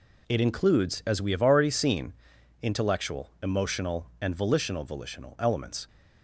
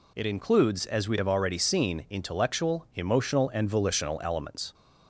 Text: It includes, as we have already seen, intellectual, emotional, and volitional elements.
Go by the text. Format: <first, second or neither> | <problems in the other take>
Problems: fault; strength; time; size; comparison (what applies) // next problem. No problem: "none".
second | says "volitional" twice; at 4.8 s